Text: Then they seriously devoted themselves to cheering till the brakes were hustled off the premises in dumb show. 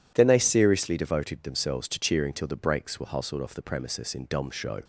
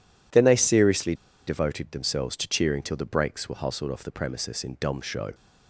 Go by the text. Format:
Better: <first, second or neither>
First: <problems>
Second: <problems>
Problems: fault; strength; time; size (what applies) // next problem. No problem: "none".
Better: first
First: none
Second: pauses between "seriously" and "devoted"; slight; at 1.1 s; 0.32 s long